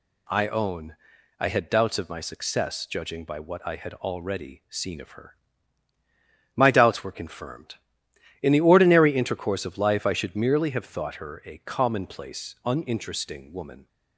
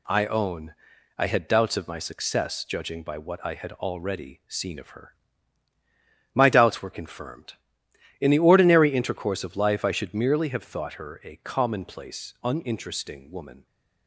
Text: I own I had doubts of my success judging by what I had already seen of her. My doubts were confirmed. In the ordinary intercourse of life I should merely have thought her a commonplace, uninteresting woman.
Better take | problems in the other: first | gets quieter; throughout; 4 dB // pauses between "own" and "I"; at 0.7 s; 0.44 s long; also in the first

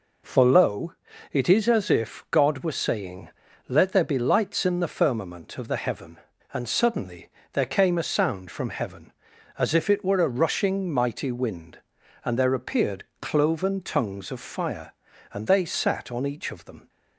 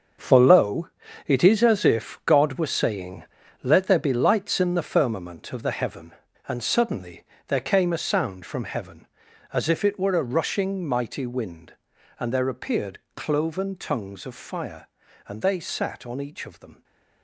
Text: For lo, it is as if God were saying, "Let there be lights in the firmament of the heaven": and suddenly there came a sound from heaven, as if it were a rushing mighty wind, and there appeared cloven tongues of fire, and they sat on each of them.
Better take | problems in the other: first | gets quieter; strong; throughout; 11 dB // pauses between "suddenly" and "there"; slight; at 7.2 s; 0.24 s long; slight in the first // pauses between "appeared" and "cloven"; slight; at 12.9 s; 0.16 s long; slight in the first // stays silent after the last word; slight; from 16.7 s on; 0.5 s long

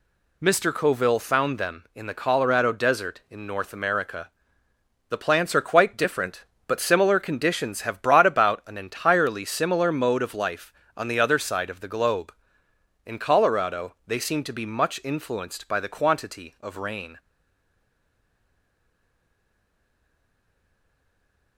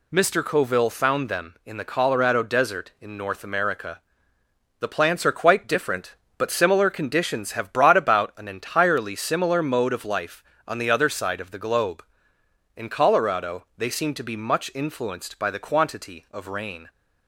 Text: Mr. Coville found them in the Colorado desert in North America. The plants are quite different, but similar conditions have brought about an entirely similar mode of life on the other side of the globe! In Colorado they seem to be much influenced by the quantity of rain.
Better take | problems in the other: second | stays silent after the last word; strong; from 17.1 s on; 4.4 s long

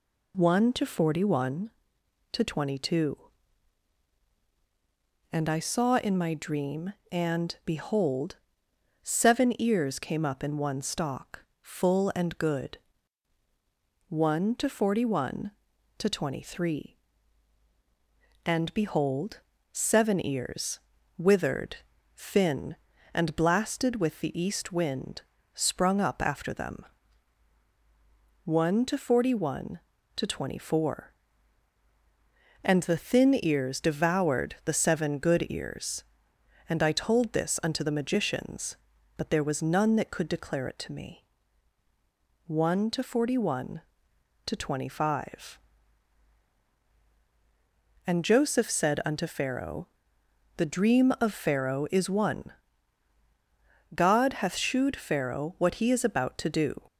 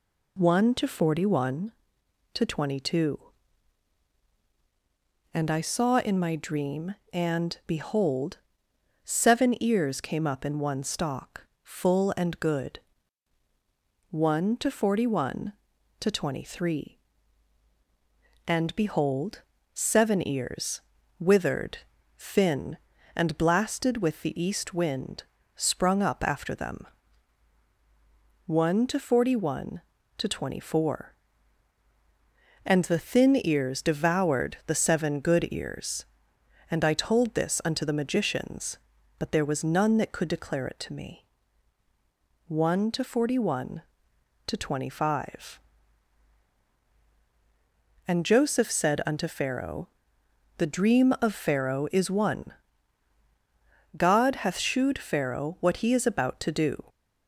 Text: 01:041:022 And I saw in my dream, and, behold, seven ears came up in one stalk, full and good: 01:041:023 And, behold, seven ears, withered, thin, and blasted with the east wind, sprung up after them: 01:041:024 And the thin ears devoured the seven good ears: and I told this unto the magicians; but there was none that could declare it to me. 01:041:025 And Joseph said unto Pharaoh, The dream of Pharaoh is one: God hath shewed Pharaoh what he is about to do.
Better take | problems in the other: neither | none

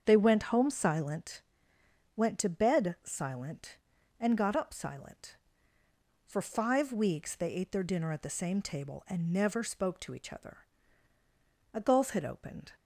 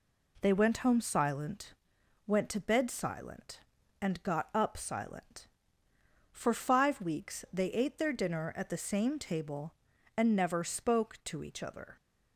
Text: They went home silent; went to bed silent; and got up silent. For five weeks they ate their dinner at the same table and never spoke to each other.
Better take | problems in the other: second | starts louder than the rest; strong; until 1.0 s; 7.5 dB // goes on to say "A gulf had opened"; noticeable; from 11.7 s on; 1.0 s long

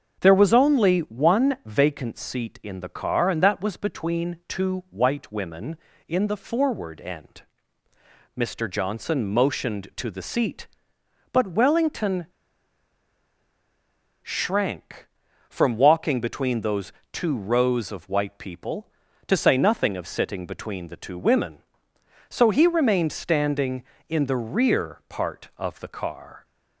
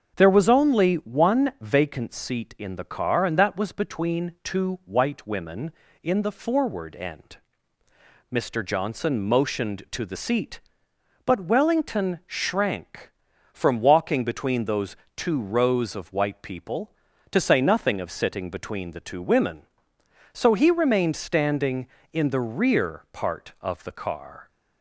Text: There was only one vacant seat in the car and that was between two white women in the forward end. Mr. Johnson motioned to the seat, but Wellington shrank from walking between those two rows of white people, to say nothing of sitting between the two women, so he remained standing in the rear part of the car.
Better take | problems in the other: second | starts louder than the rest; until 1.2 s; 6.5 dB; also in the second // pauses between "Wellington" and "shrank"; strong; at 12.2 s; 1.9 s long // pauses between "those" and "two"; slight; at 16.9 s; 0.18 s long; slight in the second

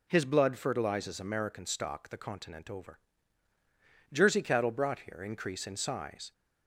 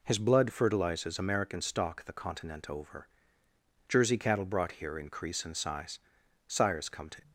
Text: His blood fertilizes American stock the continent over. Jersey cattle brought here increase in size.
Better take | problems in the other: first | goes on to say "Sires come to"; noticeable; from 6.4 s on; 0.84 s long

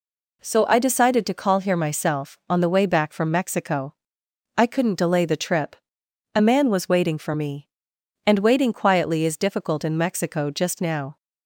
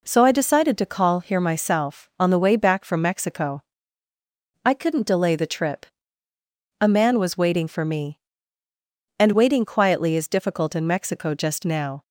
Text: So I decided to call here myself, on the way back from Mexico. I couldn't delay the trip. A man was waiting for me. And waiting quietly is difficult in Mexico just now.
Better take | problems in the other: neither | none

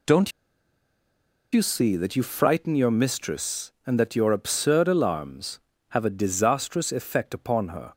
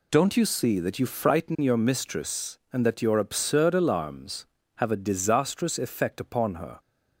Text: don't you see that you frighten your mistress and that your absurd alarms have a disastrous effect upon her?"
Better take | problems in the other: second | pauses between "don't" and "you"; at 0.3 s; 1.2 s long

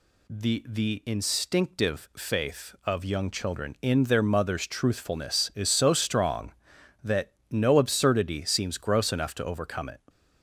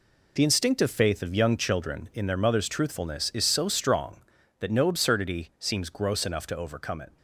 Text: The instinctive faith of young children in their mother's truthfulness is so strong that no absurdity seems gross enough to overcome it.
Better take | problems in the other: second | says "The" twice; at 0.6 s // pauses between "that" and "no"; slight; at 7.3 s; 0.20 s long

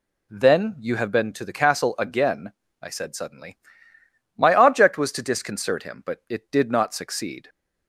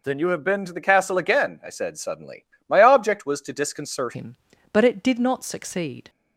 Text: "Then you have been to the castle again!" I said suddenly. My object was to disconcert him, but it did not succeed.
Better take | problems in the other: first | changes voice at "him"; from 4.1 s on; 1.9 s long

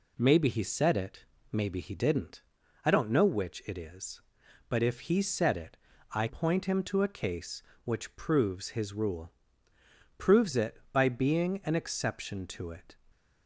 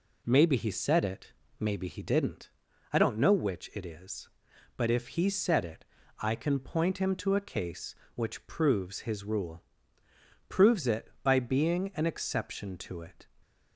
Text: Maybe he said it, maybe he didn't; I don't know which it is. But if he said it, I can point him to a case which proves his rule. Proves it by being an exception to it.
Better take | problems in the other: second | skips "can"; at 6.2 s

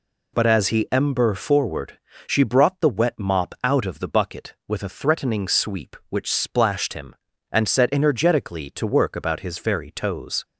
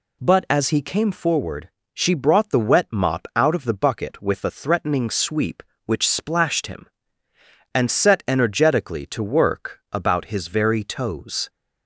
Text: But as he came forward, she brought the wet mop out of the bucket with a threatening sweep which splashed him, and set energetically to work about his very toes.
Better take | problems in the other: second | says "ember" for "came"; at 0.9 s

